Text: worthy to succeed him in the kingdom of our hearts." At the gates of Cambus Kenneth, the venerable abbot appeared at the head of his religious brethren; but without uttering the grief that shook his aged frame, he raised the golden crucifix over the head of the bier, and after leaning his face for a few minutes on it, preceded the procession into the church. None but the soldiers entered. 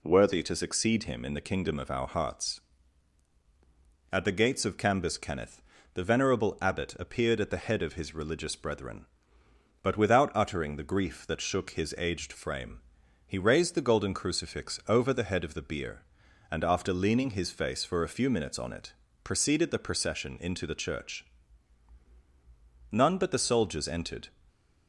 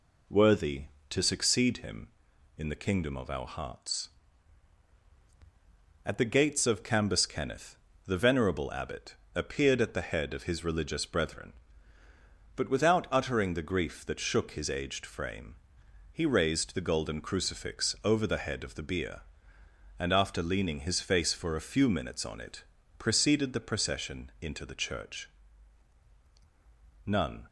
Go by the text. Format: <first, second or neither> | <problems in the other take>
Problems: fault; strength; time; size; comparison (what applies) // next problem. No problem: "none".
first | pauses between "abbot" and "appeared"; slight; at 9.1 s; 0.20 s long // stops before "but the soldiers entered"; at 27.4 s